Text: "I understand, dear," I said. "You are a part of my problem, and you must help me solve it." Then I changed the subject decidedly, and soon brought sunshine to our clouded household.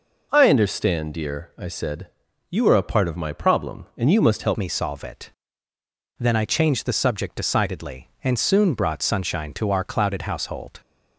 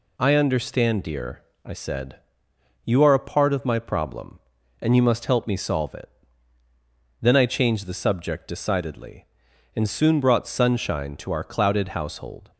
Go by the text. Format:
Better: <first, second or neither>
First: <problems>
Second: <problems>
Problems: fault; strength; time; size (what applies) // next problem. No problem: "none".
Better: second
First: changes voice at "me"; from 4.5 s on; 6.2 s long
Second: none